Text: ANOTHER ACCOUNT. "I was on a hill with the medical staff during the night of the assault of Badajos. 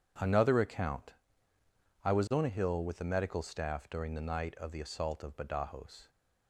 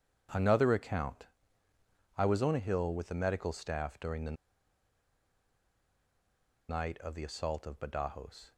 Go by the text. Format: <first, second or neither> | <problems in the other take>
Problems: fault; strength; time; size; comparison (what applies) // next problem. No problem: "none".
first | pauses between "the" and "night"; strong; at 4.3 s; 2.3 s long